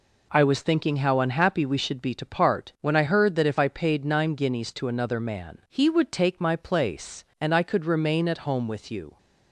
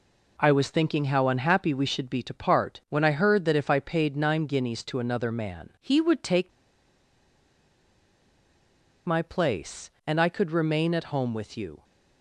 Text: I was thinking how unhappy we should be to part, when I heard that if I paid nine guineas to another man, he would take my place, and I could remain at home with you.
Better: first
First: none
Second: pauses between "take" and "my"; strong; at 6.5 s; 2.5 s long

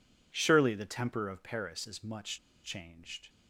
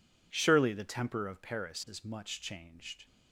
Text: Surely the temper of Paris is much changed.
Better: second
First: pauses between "much" and "changed"; slight; at 2.3 s; 0.26 s long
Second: none

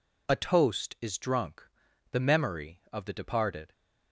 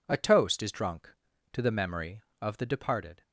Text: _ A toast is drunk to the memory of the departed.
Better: second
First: skips "to"; at 1.8 s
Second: none

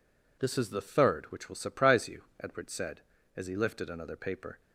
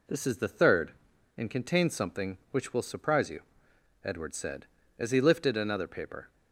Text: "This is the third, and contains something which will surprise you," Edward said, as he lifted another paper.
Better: second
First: skips "and contains something"; at 1.3 s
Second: none

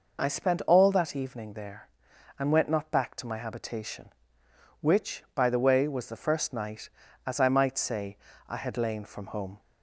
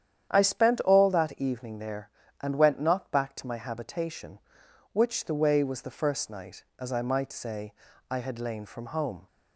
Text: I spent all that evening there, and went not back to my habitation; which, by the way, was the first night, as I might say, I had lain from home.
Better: first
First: none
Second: starts louder than the rest; strong; until 1.3 s; 9.5 dB // skips "by"; at 5.2 s

